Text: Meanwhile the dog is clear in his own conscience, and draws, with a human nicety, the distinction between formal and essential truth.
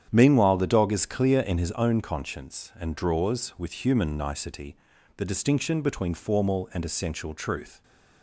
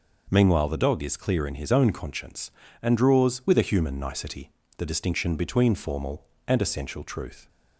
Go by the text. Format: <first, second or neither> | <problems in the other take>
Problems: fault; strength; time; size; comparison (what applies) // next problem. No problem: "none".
second | starts louder than the rest; strong; until 1.1 s; 9 dB // skips "a"; at 3.8 s